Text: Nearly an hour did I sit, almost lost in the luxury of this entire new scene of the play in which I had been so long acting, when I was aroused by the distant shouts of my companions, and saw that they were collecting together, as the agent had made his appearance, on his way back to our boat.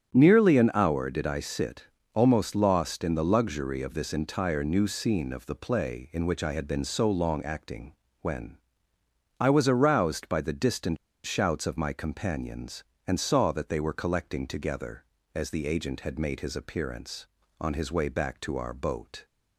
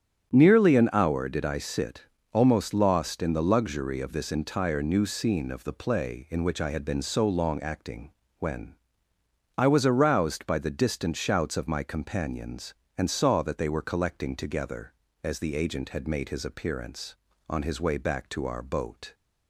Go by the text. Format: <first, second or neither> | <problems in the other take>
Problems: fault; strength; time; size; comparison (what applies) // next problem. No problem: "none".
second | starts louder than the rest; strong; until 1.1 s; 8.5 dB; strong in the second // pauses between "when" and "I"; noticeable; at 8.5 s; 0.82 s long; noticeable in the second // pauses between "distant" and "shouts"; slight; at 10.9 s; 0.29 s long